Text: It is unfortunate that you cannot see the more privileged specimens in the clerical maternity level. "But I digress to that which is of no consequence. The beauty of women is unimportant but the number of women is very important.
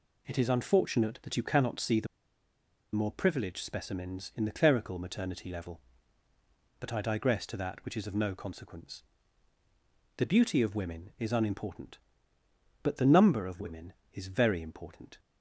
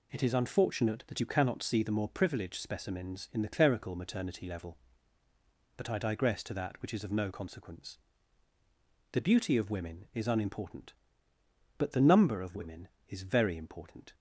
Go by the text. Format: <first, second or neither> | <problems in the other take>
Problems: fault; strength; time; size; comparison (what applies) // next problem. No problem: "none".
second | pauses between "the" and "more"; noticeable; at 2.0 s; 0.88 s long